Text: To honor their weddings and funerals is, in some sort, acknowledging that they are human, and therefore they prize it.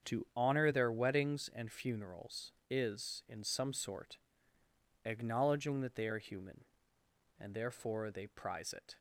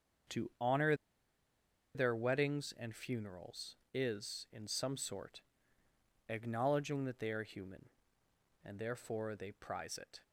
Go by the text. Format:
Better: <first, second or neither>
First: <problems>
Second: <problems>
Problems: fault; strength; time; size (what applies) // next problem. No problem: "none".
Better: first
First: starts louder than the rest; strong; until 1.1 s; 7 dB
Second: starts louder than the rest; until 2.4 s; 7 dB // pauses between "honor" and "their"; at 0.9 s; 1.0 s long